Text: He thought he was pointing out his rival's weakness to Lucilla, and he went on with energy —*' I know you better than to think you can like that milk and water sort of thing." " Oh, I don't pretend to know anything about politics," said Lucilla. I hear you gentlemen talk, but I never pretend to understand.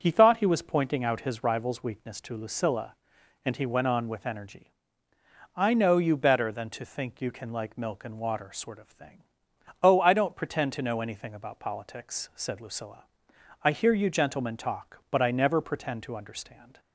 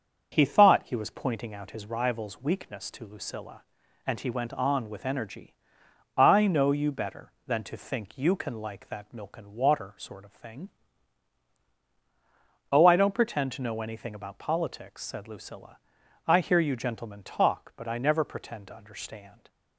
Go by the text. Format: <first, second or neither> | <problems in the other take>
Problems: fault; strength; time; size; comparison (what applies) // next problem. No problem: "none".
second | starts louder than the rest; strong; until 1.0 s; 7 dB; also in the second // skips "that"; at 7.7 s